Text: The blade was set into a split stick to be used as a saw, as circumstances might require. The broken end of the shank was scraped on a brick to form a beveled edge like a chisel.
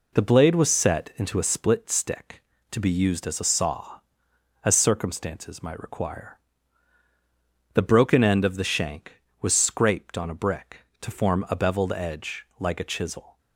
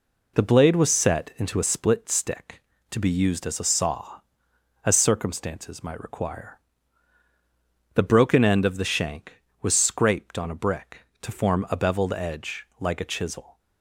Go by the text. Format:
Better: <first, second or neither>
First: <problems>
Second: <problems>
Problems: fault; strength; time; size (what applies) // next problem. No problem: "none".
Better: neither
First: none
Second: none